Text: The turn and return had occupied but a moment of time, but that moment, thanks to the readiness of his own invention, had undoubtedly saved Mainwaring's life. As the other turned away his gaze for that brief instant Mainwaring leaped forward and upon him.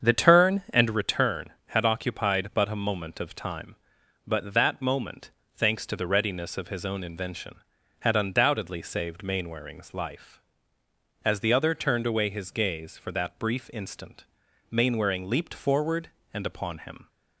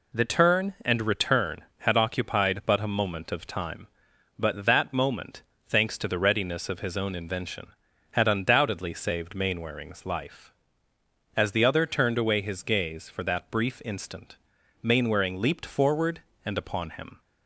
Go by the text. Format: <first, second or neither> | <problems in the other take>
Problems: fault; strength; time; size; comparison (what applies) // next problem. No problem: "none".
second | starts louder than the rest; strong; until 0.9 s; 7.5 dB // pauses between "instant" and "Mainwaring"; noticeable; at 14.2 s; 0.46 s long; noticeable in the second